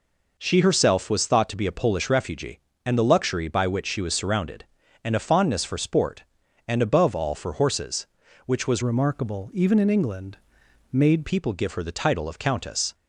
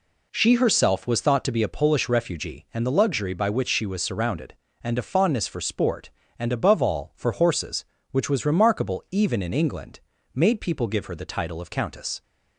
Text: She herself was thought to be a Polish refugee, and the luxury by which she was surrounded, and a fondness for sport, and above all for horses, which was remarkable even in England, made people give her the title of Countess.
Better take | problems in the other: second | changes voice from "remarkable" to "made"; from 8.8 to 11.2 s; 2.4 s long

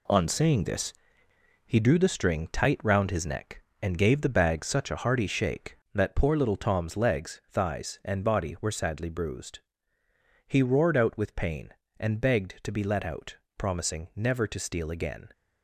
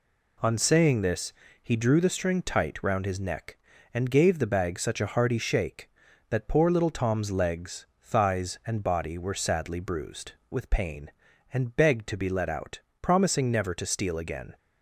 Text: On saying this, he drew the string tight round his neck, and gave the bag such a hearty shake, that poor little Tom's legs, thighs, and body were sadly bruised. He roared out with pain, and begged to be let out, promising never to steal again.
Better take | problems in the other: first | skips "He roared out"; at 10.4 s

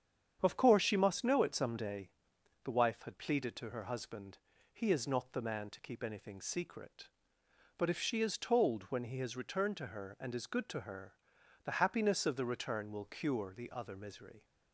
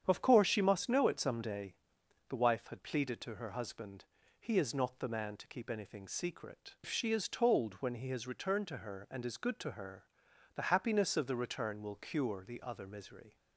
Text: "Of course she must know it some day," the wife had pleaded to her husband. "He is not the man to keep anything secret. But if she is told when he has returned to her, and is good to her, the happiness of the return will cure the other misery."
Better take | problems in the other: first | starts louder than the rest; strong; until 1.0 s; 9 dB; strong in the first // skips "But"; at 6.7 s

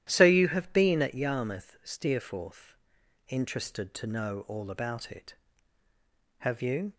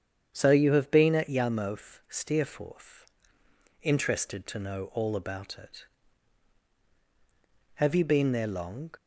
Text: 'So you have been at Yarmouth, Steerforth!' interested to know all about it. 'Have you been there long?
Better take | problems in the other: second | starts louder than the rest; strong; until 1.1 s; 12 dB; strong in the second // stops before "been there long"; at 6.9 s

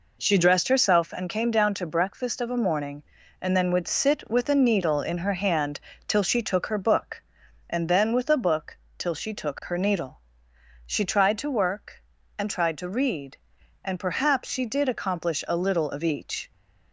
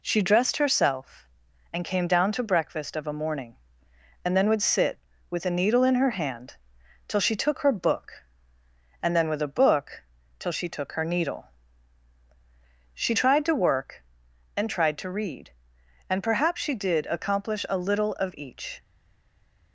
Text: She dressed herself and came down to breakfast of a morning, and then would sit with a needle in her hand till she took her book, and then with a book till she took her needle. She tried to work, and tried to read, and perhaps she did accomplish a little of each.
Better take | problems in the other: first | pauses between "hand" and "till"; noticeable; at 6.5 s; 0.50 s long; slight in the first // pauses between "book" and "till"; slight; at 10.0 s; 0.36 s long; slight in the first // stays silent after the last word; slight; from 18.8 s on; 0.9 s long

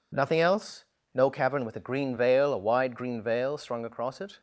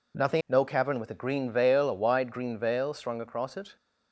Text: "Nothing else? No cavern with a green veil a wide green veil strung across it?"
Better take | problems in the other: first | skips "else"; at 0.4 s

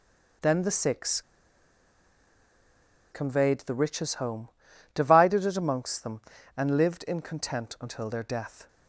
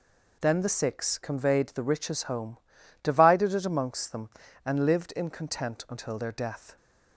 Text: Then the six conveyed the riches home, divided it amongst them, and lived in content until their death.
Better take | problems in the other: second | pauses between "six" and "conveyed"; strong; at 1.2 s; 1.9 s long

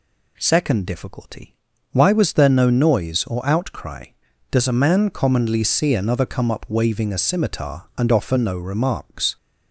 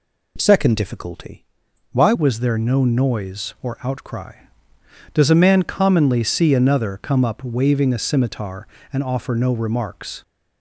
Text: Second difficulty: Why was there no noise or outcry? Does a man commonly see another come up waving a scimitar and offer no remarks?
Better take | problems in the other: first | changes voice at "was"; from 2.1 s on; 8.1 s long

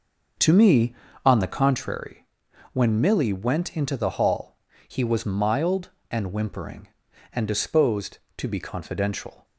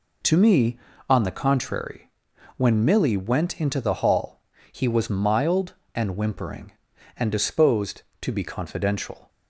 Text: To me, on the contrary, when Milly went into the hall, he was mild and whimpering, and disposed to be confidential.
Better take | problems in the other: second | starts louder than the rest; noticeable; until 1.8 s; 6 dB

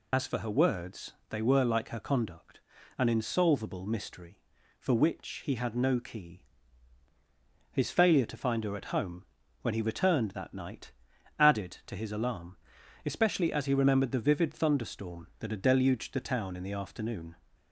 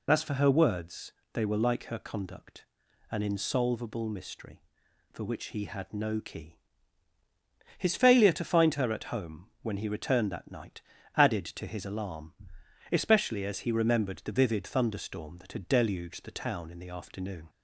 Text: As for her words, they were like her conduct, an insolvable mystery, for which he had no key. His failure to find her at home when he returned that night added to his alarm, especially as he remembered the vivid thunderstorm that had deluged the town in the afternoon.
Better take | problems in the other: second | loses the start of "As"; at 0.1 s; 60 ms // pauses between "home" and "when"; at 9.2 s; 0.38 s long; slight in the second // pauses between "night" and "added"; noticeable; at 10.9 s; 0.46 s long; slight in the second

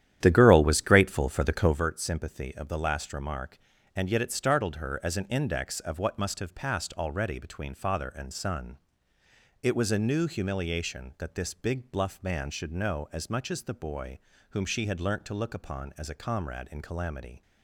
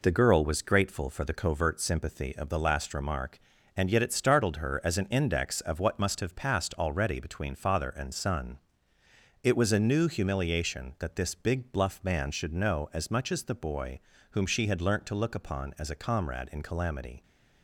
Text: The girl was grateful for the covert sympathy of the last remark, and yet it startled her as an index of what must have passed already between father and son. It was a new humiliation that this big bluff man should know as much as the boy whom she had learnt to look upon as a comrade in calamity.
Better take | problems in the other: second | starts louder than the rest; strong; until 1.8 s; 11 dB // pauses between "boy" and "whom"; slight; at 14.1 s; 0.32 s long; slight in the second

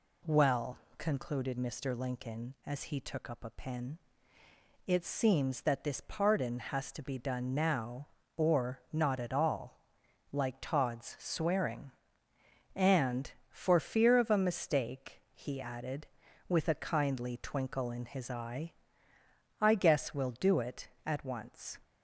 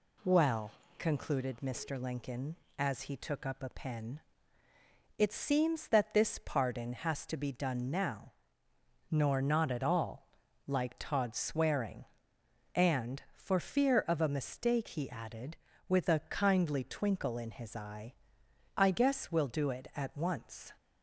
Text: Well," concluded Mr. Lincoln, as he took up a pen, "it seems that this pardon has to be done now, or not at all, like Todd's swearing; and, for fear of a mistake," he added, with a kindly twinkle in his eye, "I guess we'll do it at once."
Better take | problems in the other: first | says "nor" for "or"; at 9.0 s

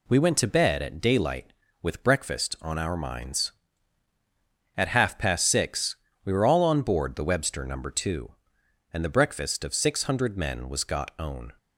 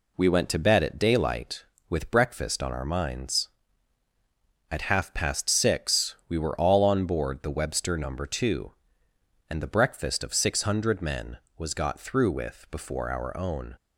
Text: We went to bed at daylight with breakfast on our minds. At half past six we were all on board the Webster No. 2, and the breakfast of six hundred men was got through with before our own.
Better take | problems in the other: second | pauses between "six" and "we"; slight; at 5.9 s; 0.26 s long // skips "through with before our"; at 11.1 s

